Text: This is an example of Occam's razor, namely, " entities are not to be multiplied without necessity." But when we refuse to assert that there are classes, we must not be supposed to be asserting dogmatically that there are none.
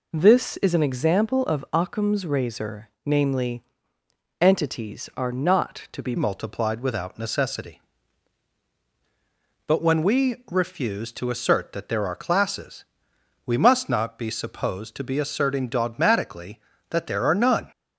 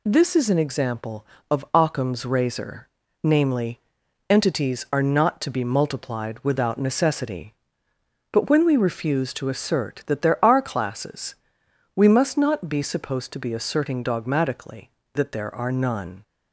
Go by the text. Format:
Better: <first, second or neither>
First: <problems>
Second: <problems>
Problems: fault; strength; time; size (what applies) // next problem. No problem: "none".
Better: second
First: changes voice at "multiplied"; from 6.1 s on; 11.6 s long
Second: none